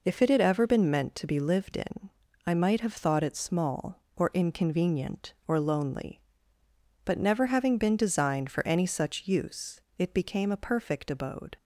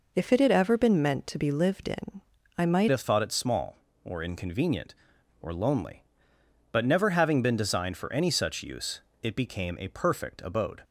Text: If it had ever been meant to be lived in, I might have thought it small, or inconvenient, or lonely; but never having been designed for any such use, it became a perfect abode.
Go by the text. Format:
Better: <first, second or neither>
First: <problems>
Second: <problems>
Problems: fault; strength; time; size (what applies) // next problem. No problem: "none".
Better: first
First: none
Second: changes voice at "have"; from 2.9 s on; 7.9 s long